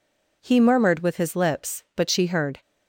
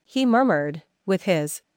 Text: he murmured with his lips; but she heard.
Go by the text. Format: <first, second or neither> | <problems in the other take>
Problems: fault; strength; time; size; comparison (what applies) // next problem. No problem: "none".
first | stops before "lips but she heard"; at 1.6 s